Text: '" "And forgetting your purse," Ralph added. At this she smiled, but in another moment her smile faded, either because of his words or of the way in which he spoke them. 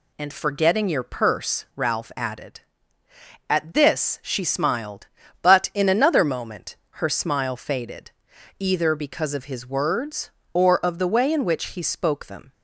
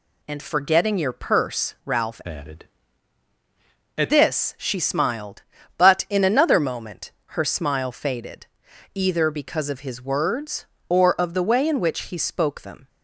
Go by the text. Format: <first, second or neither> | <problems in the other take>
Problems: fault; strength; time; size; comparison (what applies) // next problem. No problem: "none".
first | changes voice from "added" to "At"; from 2.2 to 4.1 s; 1.9 s long // pauses between "moment" and "her"; slight; at 7.1 s; 0.22 s long; slight in the first